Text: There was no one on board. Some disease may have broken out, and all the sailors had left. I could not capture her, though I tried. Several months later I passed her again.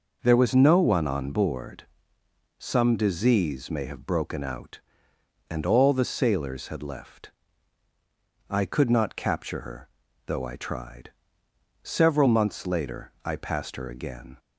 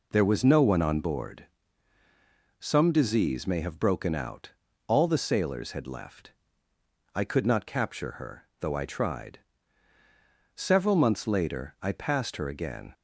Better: first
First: none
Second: skips "and"; at 4.6 s

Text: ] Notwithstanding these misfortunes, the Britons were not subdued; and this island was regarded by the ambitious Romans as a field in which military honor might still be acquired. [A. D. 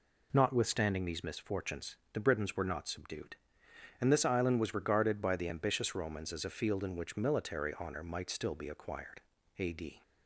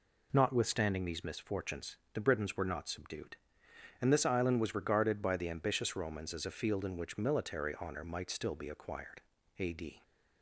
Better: neither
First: none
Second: none

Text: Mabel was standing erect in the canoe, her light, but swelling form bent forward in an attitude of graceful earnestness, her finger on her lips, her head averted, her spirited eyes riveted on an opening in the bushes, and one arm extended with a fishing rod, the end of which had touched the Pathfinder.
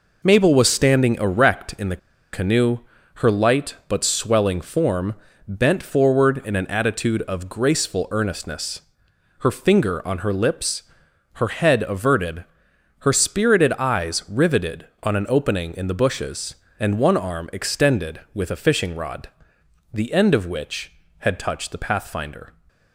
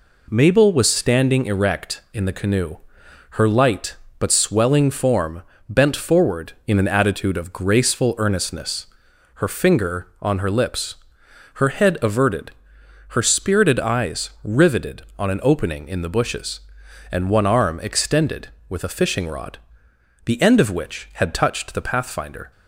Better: second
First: pauses between "the" and "canoe"; slight; at 1.9 s; 0.35 s long // pauses between "form" and "bent"; slight; at 5.1 s; 0.32 s long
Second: pauses between "form" and "bent"; slight; at 5.4 s; 0.26 s long

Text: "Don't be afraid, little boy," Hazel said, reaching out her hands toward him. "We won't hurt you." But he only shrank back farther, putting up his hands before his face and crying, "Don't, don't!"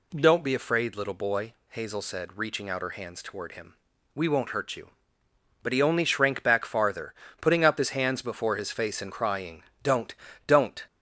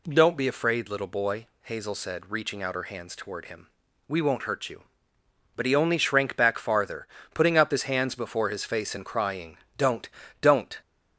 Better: neither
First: none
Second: none

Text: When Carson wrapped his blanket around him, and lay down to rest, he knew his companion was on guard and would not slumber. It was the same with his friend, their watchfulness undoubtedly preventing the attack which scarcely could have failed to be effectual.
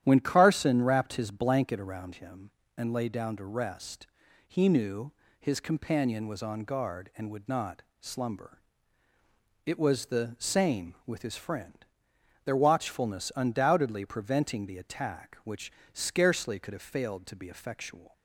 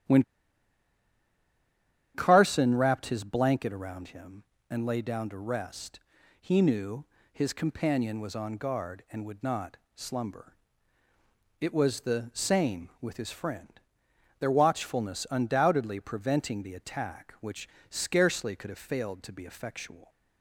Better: first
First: starts louder than the rest; strong; until 1.0 s; 11 dB // pauses between "knew" and "his"; slight; at 5.1 s; 0.28 s long // pauses between "not" and "slumber"; slight; at 7.8 s; 0.18 s long // pauses between "which" and "scarcely"; slight; at 15.7 s; 0.22 s long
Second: starts louder than the rest; strong; until 2.9 s; 11 dB // pauses between "When" and "Carson"; strong; at 0.2 s; 1.9 s long // pauses between "knew" and "his"; slight; at 7.0 s; 0.28 s long // pauses between "not" and "slumber"; slight; at 9.7 s; 0.18 s long // pauses between "which" and "scarcely"; slight; at 17.6 s; 0.22 s long

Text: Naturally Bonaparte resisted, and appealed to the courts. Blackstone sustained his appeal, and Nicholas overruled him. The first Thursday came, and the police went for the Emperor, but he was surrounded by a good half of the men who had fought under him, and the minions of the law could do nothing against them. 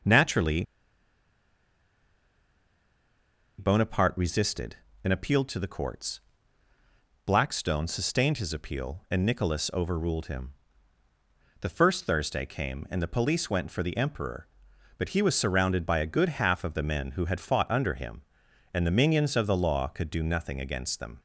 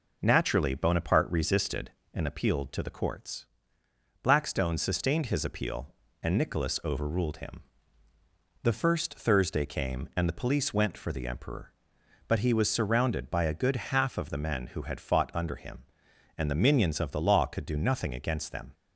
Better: second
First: pauses between "Naturally" and "Bonaparte"; strong; at 0.6 s; 2.9 s long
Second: none

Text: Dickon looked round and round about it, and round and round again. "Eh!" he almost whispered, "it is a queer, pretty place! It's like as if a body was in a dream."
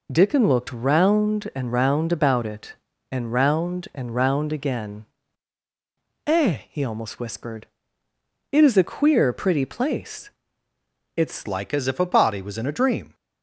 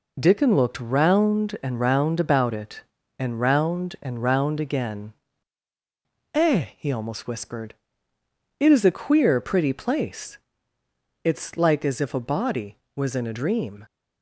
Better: second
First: changes voice at "like"; from 11.4 s on; 1.7 s long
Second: none

